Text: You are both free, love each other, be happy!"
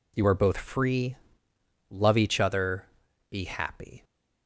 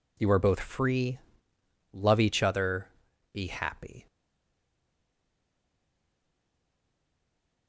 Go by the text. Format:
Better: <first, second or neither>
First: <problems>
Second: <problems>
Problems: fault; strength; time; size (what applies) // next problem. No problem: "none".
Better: first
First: none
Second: stays silent after the last word; strong; from 4.0 s on; 3.6 s long